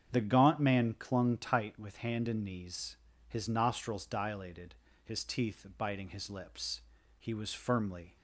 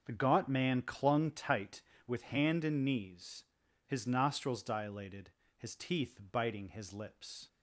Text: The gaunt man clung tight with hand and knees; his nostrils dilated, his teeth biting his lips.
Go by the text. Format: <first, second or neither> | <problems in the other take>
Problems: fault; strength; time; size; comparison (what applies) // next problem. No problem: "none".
second | starts louder than the rest; strong; until 1.1 s; 8 dB // goes on to say "He was firmly"; noticeable; from 7.2 s on; 0.96 s long